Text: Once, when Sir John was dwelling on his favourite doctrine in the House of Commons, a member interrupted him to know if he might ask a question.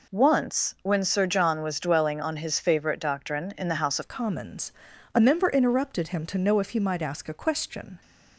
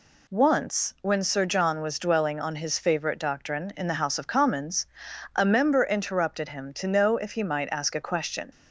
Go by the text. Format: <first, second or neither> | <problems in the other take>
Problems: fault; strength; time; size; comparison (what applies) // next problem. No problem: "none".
second | changes voice at "of"; from 4.0 s on; 4.0 s long